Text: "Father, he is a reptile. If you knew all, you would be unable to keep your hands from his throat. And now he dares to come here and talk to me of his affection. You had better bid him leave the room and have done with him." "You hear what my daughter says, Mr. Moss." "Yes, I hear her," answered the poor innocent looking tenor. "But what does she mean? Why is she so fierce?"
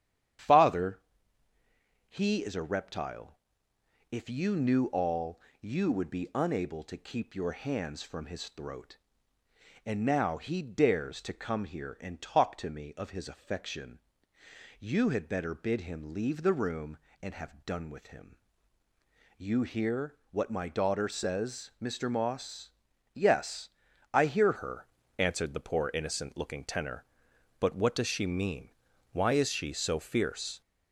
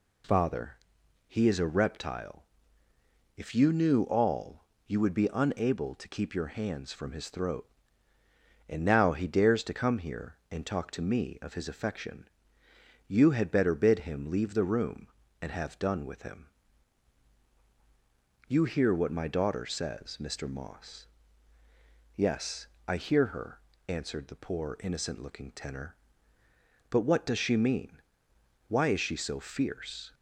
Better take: second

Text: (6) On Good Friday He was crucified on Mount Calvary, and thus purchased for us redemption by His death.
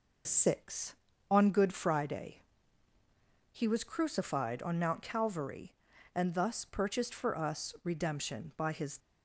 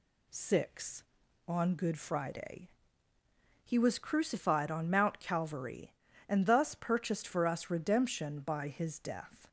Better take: second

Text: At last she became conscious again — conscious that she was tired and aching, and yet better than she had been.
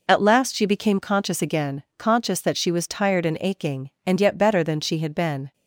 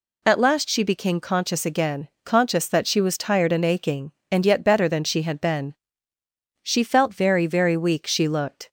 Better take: first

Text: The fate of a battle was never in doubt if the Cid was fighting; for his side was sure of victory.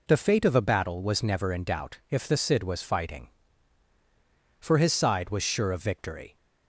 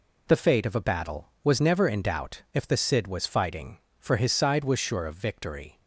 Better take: neither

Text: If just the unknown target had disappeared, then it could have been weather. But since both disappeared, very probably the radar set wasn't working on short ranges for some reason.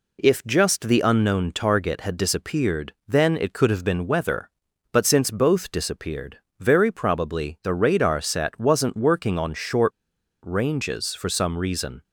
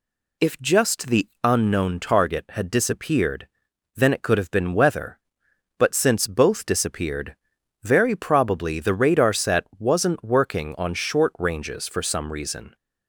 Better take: second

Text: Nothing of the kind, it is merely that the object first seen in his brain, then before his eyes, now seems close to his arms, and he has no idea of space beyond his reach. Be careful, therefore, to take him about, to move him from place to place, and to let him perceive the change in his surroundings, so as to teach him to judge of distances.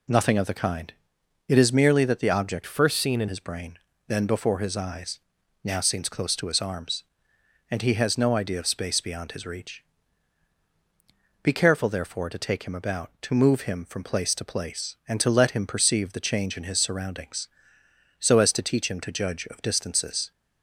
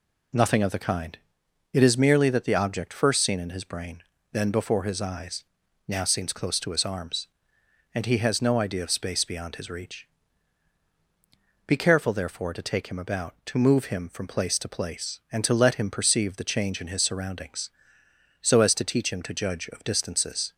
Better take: second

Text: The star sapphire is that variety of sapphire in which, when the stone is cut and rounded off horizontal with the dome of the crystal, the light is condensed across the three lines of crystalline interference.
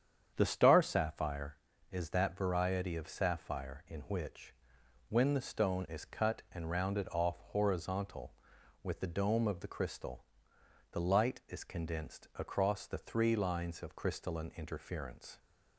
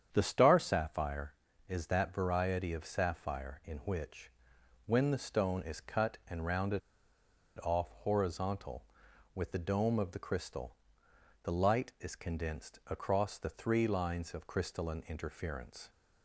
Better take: first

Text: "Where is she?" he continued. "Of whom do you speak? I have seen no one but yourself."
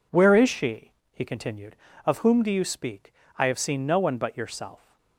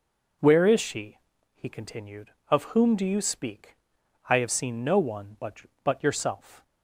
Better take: first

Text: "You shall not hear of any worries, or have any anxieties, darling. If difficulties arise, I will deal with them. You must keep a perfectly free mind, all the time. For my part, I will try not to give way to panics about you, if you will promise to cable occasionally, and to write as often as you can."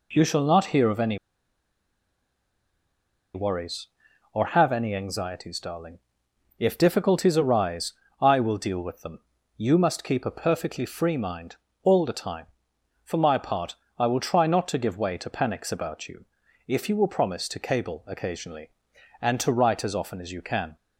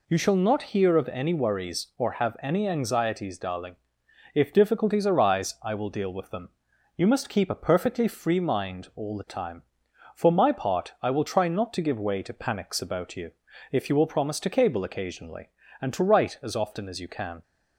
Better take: second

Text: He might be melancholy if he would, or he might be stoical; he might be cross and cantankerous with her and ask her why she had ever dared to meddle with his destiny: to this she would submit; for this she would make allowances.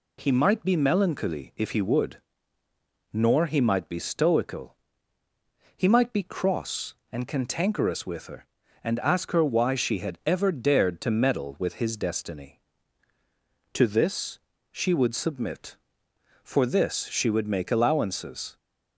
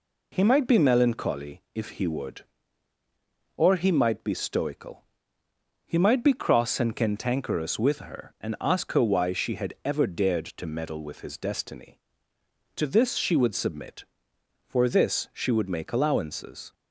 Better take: second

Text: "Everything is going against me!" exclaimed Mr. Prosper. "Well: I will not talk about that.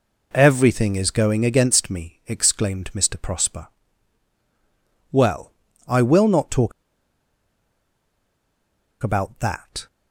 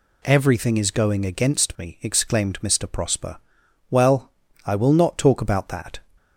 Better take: second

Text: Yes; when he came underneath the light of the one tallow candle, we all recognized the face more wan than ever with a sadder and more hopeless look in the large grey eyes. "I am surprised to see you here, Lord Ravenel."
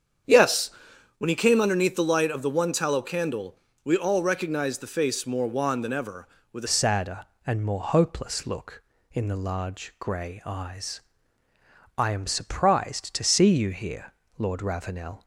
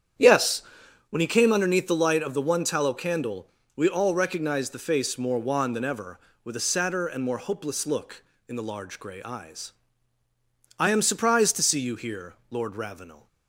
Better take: second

